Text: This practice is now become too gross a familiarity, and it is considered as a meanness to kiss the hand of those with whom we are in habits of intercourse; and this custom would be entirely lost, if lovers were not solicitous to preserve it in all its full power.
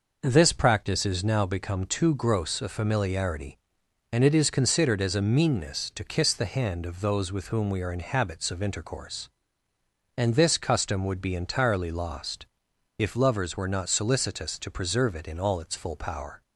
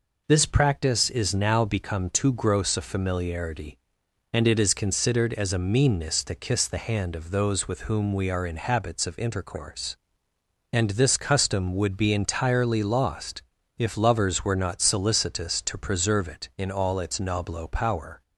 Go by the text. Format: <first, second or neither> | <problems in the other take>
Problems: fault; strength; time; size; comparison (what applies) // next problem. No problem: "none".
first | says "noblo" for "full"; at 17.1 s